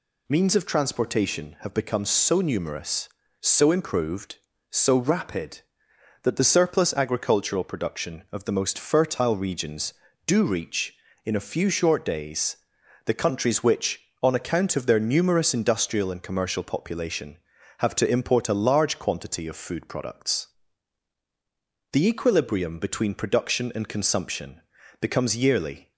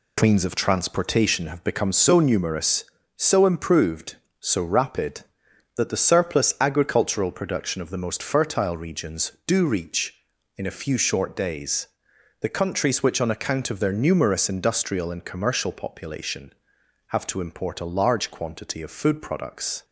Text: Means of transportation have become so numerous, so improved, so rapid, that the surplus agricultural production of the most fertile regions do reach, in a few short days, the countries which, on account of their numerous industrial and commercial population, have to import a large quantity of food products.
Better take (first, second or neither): second